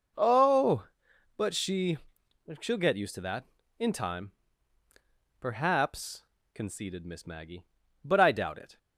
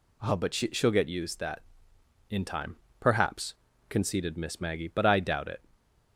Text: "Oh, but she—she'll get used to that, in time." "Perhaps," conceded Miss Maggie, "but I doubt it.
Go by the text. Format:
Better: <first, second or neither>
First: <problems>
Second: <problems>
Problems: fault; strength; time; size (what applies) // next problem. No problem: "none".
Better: first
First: none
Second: skips "to"; at 1.3 s